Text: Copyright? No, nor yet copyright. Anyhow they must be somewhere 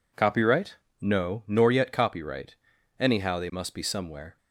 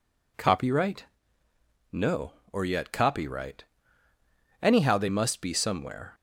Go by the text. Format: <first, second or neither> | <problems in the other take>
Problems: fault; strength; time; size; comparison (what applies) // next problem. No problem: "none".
first | says "or" for "nor"; at 2.5 s